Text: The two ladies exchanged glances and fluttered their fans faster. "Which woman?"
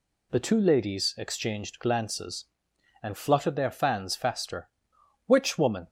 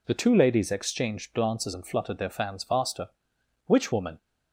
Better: neither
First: none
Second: none

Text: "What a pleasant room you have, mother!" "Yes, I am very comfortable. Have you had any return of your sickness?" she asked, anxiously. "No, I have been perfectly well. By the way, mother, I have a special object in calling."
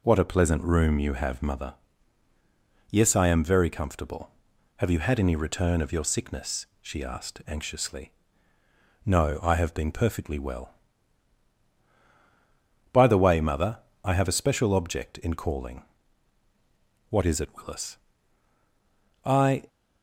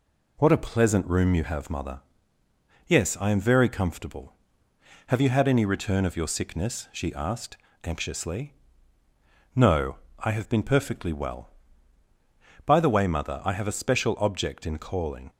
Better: second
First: goes on to say "What is it Willis I"; strong; from 17.0 s on; 2.5 s long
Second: none

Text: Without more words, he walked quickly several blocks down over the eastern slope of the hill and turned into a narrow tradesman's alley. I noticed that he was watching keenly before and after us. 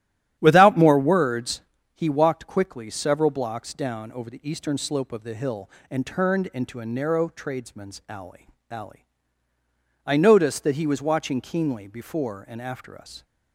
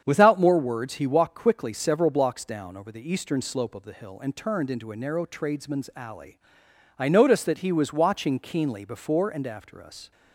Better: second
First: starts louder than the rest; strong; until 1.4 s; 11 dB // says "alley" twice; at 8.6 s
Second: starts louder than the rest; strong; until 1.0 s; 7.5 dB

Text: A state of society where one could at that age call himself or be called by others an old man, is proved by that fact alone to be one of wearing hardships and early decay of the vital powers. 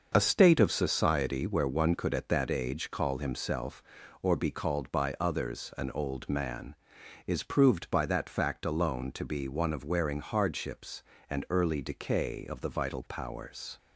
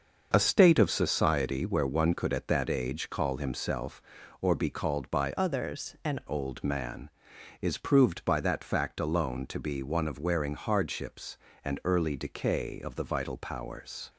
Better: first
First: starts louder than the rest; noticeable; until 1.1 s; 6 dB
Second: starts louder than the rest; noticeable; until 1.3 s; 6 dB // changes voice from "others" to "an"; from 5.3 to 6.1 s; 0.8 s long

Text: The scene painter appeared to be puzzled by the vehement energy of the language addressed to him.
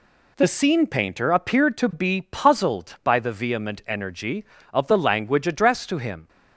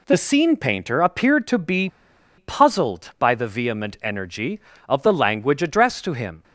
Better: first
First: none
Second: pauses between "be" and "puzzled"; noticeable; at 1.8 s; 0.49 s long

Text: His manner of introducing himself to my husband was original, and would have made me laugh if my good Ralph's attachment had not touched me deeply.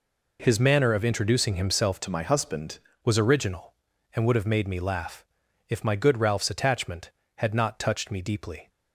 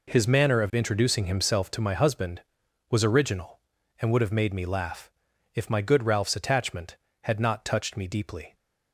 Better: second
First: changes voice from "to" to "husband"; from 2.0 to 2.7 s; 0.7 s long // pauses between "laugh" and "if"; noticeable; at 5.2 s; 0.46 s long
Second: pauses between "laugh" and "if"; noticeable; at 5.0 s; 0.46 s long

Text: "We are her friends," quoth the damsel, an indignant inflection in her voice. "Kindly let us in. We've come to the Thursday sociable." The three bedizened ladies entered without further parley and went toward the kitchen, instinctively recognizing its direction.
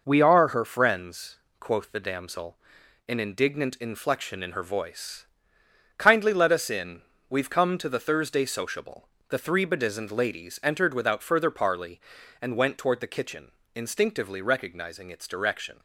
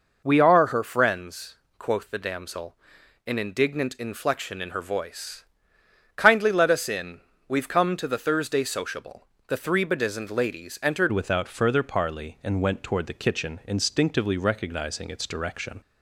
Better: first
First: none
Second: changes voice at "without"; from 11.1 s on; 4.7 s long

